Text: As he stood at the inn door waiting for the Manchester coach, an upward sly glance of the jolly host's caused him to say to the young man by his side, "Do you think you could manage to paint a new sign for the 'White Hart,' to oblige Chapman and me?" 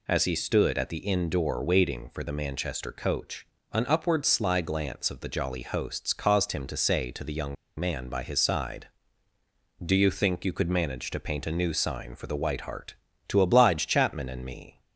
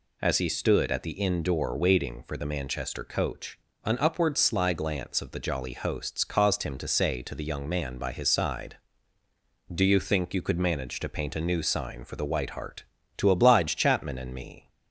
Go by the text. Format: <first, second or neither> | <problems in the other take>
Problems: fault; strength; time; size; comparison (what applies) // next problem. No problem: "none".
second | pauses between "young" and "man"; slight; at 7.5 s; 0.24 s long